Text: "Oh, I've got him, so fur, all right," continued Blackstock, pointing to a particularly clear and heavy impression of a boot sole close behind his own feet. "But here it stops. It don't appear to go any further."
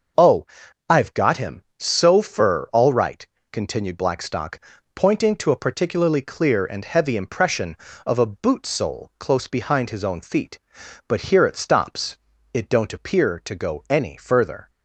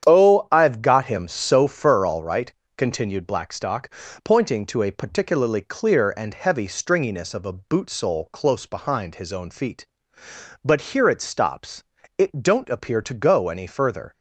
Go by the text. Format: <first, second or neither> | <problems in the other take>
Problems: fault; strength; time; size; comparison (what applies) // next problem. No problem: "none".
first | starts louder than the rest; strong; until 1.1 s; 9 dB; noticeable in the first // says "stringiness" for "impression"; at 6.6 s